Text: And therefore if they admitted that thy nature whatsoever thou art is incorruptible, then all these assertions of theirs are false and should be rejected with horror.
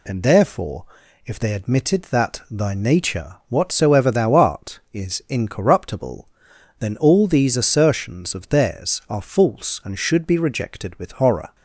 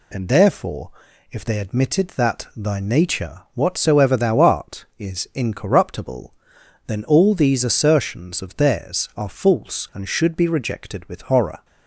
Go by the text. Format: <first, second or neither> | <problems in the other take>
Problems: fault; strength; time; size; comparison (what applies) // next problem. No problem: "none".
neither | pauses between "therefore" and "if"; the same in both